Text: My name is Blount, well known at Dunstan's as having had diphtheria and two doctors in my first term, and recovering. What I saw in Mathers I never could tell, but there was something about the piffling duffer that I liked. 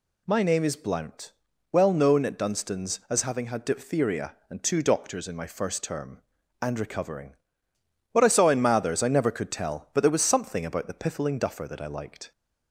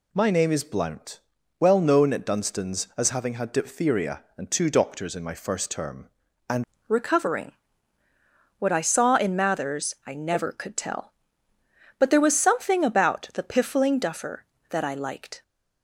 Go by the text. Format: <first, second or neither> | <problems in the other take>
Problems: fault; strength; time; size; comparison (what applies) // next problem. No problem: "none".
first | changes voice at "recovering"; from 6.8 s on; 8.6 s long